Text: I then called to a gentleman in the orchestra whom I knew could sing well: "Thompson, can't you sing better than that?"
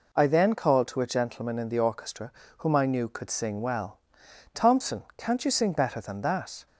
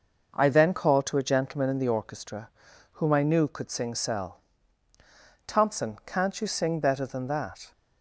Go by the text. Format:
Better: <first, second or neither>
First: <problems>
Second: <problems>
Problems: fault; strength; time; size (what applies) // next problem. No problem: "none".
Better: first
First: pauses between "orchestra" and "whom"; slight; at 2.3 s; 0.26 s long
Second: pauses between "orchestra" and "whom"; at 2.4 s; 0.44 s long // says "cell" for "well"; at 3.9 s